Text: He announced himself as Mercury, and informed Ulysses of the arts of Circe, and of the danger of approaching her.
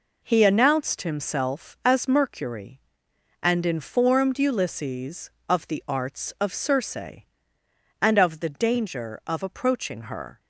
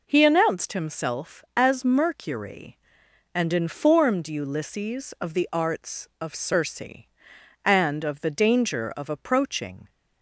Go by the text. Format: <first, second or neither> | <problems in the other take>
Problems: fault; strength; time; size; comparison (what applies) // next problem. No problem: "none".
first | stops before "her"; at 9.8 s